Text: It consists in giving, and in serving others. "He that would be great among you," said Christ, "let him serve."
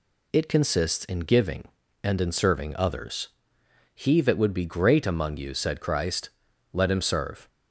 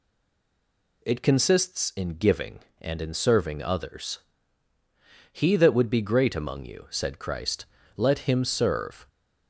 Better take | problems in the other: first | stays silent before the first word; until 1.0 s; 1.0 s long

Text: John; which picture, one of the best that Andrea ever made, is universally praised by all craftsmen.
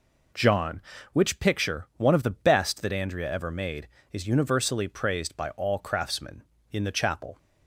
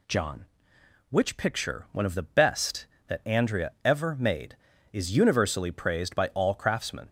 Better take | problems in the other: second | goes on to say "In the Chapel"; noticeable; from 6.7 s on; 0.66 s long

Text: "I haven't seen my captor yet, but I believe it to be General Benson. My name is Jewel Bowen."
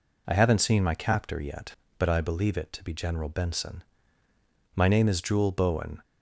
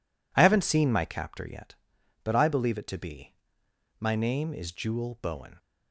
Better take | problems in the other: first | skips "General Benson"; at 3.6 s

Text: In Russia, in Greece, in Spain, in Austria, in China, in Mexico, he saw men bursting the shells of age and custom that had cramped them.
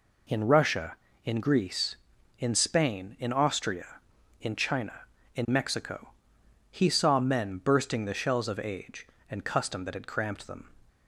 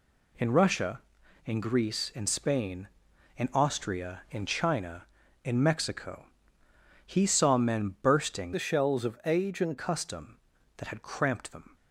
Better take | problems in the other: first | changes voice from "the" to "and"; from 8.5 to 9.7 s; 1.2 s long

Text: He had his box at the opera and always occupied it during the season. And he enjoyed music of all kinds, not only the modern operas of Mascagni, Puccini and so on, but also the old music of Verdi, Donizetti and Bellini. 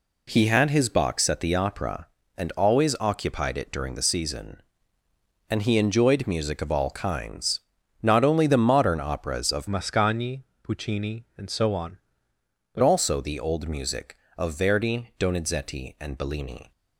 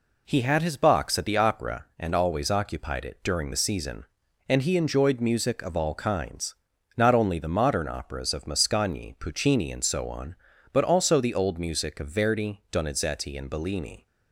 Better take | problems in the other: second | changes voice from "Mascagni" to "but"; from 9.6 to 12.8 s; 3.2 s long

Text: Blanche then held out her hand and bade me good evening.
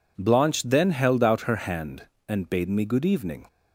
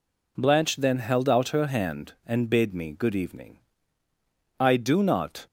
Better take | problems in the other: first | goes on to say "I do not"; noticeable; from 4.6 s on; 0.86 s long

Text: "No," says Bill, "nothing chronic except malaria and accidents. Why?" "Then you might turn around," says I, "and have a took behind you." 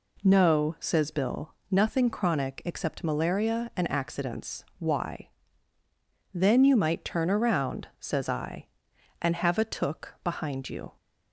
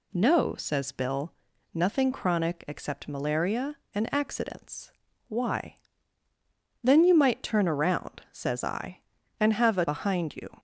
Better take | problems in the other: first | skips "took"; at 9.8 s

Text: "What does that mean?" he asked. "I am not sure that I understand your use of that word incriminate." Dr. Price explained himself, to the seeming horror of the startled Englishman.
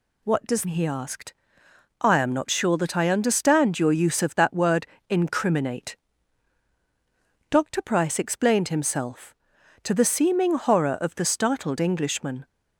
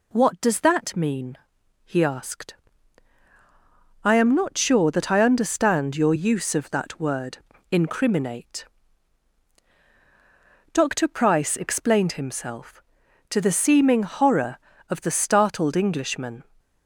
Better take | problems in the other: second | skips "that mean"; at 0.6 s // pauses between "word" and "incriminate"; slight; at 4.8 s; 0.24 s long; slight in the second

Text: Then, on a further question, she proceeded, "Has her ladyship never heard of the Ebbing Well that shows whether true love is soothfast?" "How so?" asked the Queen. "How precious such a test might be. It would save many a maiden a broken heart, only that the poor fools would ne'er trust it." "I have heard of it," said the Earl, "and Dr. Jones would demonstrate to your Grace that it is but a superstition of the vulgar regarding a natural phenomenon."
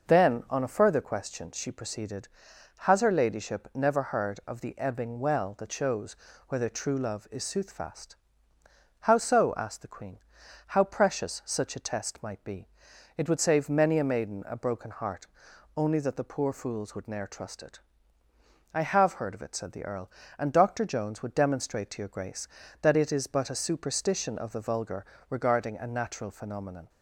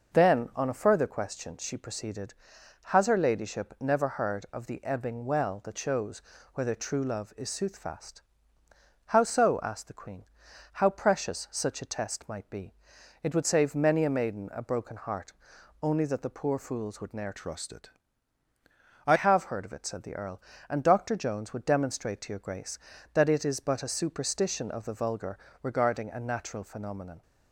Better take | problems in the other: first | pauses between "shows" and "whether"; slight; at 6.2 s; 0.32 s long; slight in the first // changes voice from "trust" to "I"; from 17.3 to 19.1 s; 1.8 s long // pauses between "vulgar" and "regarding"; slight; at 25.3 s; 0.28 s long; slight in the first

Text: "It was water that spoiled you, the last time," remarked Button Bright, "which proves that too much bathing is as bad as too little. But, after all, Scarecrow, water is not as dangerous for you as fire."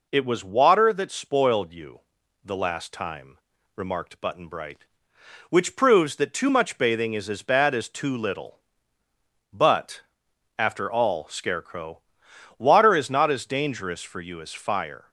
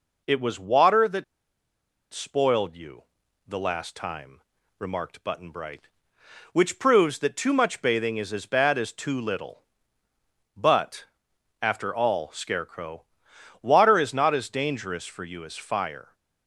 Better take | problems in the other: first | pauses between "that" and "spoiled"; noticeable; at 1.2 s; 0.89 s long

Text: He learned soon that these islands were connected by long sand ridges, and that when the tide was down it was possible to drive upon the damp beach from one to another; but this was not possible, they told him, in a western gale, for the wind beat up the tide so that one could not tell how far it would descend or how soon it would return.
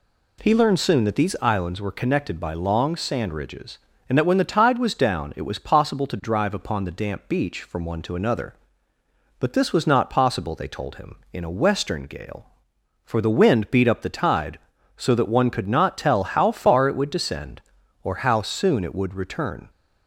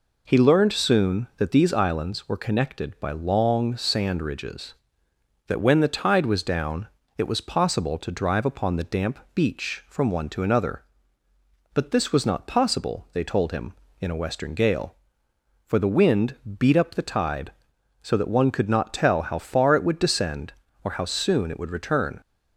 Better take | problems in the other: first | skips "and"; at 5.0 s // pauses between "down" and "it"; slight; at 6.8 s; 0.28 s long // pauses between "damp" and "beach"; slight; at 9.1 s; 0.16 s long // pauses between "wind" and "beat"; slight; at 16.3 s; 0.22 s long

